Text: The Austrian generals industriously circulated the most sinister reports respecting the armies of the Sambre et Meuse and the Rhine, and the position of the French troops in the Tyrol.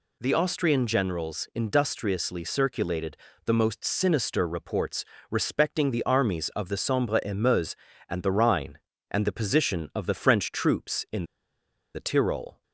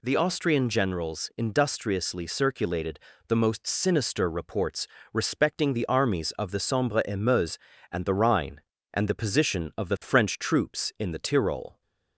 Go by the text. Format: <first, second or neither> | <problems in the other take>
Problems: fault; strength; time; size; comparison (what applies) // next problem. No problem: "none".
second | pauses between "circulated" and "the"; slight; at 3.1 s; 0.30 s long; slight in the second // pauses between "reports" and "respecting"; slight; at 5.0 s; 0.26 s long; slight in the second // pauses between "in" and "the"; noticeable; at 11.2 s; 0.70 s long